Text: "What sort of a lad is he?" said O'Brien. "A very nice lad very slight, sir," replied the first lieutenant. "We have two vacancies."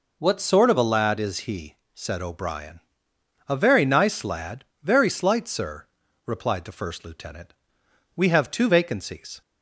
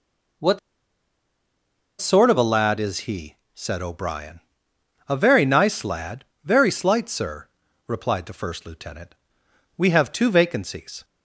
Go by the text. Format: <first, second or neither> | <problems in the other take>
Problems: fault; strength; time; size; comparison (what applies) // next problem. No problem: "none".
first | pauses between "What" and "sort"; strong; at 0.5 s; 1.4 s long // pauses between "lad" and "very"; slight; at 6.2 s; 0.18 s long; slight in the first